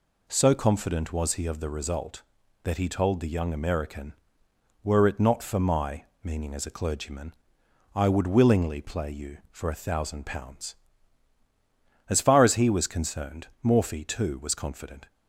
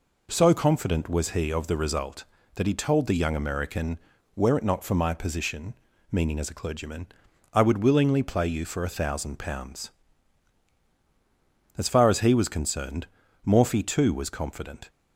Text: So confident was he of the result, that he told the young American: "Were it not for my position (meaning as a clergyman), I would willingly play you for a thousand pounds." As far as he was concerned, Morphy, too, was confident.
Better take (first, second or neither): second